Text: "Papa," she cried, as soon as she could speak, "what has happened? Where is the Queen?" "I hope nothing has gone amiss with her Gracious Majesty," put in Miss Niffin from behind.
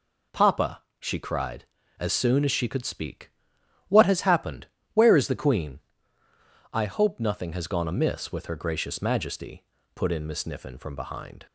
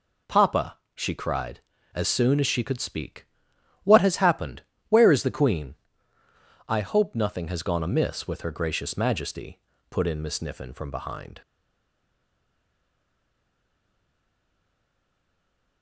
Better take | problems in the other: first | stays silent after the last word; strong; from 11.4 s on; 4.4 s long

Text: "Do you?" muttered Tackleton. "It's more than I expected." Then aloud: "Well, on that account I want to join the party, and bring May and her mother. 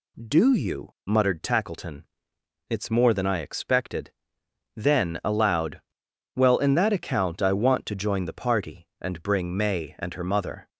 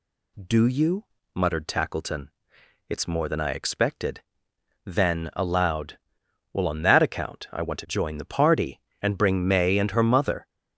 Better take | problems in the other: second | says "in" for "on"; at 6.5 s

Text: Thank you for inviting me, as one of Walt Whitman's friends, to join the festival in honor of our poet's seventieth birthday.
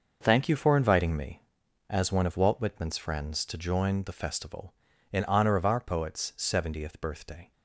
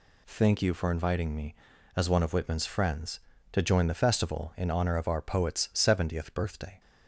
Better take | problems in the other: first | skips "Walt"; at 2.3 s

